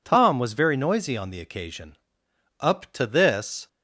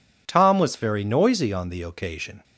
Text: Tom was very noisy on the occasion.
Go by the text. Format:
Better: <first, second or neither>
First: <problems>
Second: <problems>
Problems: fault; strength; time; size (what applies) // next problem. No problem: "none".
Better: second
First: goes on to say "Up to this"; noticeable; from 2.5 s on; 1.0 s long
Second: none